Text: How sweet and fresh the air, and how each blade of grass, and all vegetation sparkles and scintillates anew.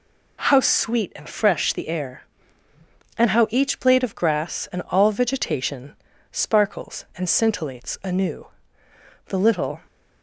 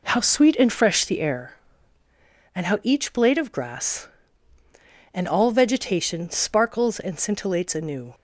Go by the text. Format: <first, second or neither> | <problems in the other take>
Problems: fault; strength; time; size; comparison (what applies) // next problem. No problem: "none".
second | pauses between "vegetation" and "sparkles"; slight; at 5.9 s; 0.35 s long // goes on to say "The little"; from 9.2 s on; 0.54 s long